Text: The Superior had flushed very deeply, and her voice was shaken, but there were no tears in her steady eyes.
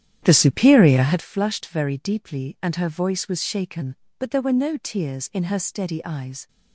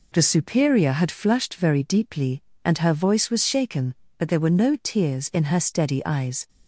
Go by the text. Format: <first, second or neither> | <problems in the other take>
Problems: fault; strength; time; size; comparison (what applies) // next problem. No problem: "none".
second | starts louder than the rest; strong; until 1.2 s; 10 dB